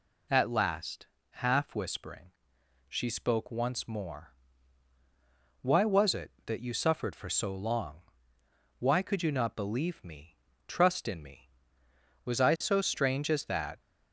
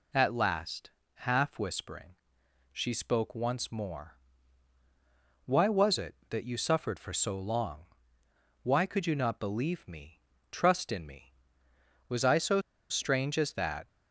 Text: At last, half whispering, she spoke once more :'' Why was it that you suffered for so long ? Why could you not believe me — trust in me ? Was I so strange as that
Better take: first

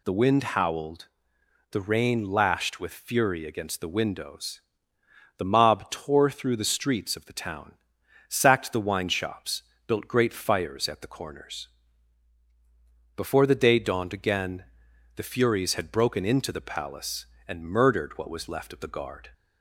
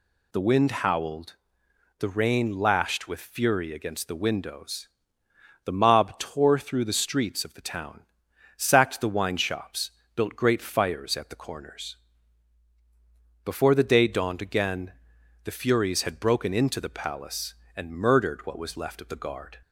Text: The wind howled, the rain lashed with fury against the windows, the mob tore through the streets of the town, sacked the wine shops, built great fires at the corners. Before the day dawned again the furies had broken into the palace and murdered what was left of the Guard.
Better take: neither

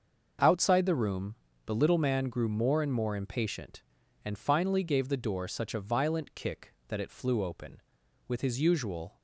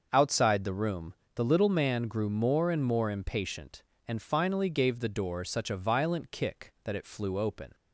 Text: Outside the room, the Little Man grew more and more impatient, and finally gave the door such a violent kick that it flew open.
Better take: second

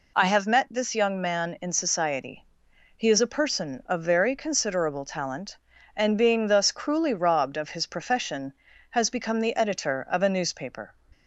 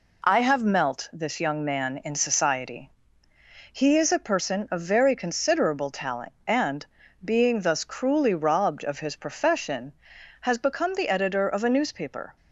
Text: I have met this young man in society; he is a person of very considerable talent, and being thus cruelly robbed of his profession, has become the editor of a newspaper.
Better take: first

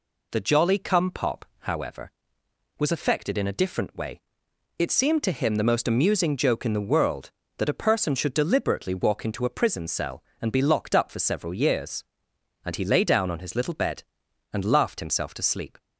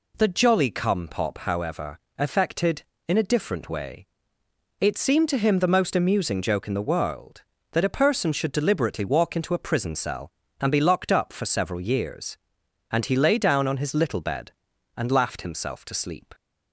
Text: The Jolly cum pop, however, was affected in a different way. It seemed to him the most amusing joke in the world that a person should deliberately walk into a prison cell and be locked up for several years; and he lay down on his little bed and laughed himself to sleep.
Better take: first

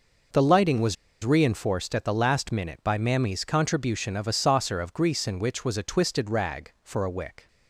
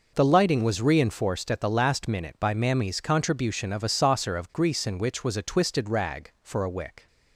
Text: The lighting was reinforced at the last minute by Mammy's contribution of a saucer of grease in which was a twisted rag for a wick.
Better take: second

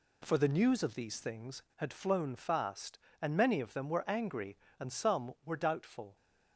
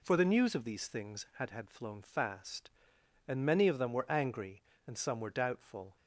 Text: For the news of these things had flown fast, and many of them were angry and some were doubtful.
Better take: first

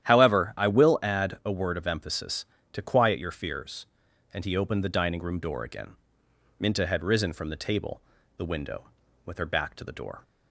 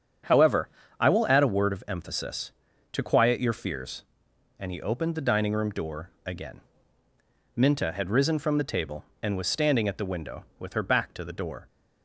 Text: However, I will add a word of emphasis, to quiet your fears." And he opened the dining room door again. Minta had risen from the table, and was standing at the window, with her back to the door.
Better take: second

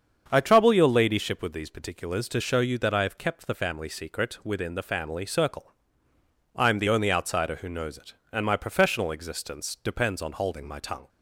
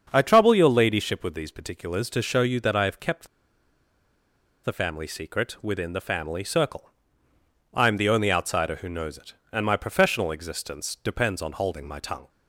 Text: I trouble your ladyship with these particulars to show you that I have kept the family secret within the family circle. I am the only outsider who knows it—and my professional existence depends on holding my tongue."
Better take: first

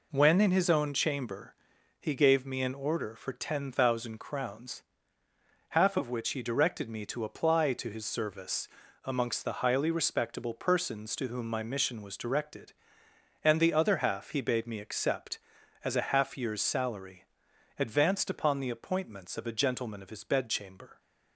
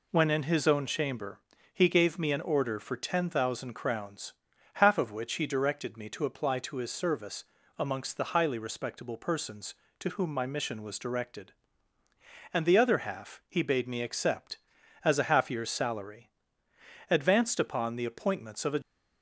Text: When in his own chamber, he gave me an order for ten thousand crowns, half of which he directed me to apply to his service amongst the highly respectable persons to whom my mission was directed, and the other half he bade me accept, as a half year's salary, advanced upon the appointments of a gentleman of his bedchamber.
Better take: first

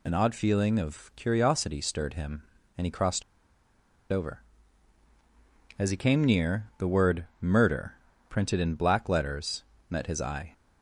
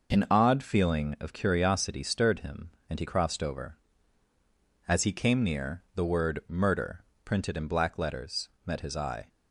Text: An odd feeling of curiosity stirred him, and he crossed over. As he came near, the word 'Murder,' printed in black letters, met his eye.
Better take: second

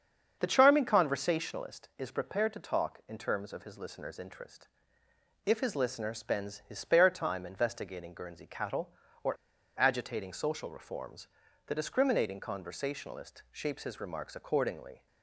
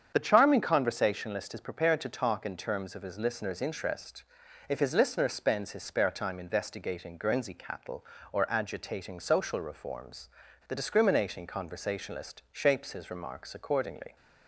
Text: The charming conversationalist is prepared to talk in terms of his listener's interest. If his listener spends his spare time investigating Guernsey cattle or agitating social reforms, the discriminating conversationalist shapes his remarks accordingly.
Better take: second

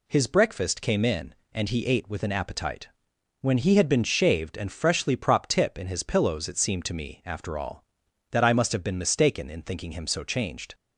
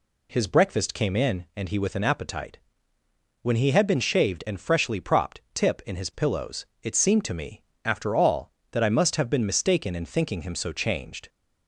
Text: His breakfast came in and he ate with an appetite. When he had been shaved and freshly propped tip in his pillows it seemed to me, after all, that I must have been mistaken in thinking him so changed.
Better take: first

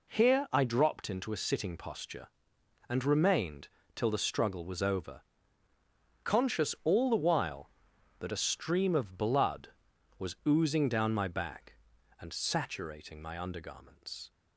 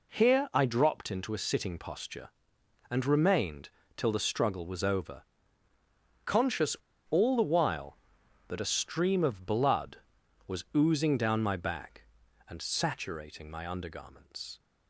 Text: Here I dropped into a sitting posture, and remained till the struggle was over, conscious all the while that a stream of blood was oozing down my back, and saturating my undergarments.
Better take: first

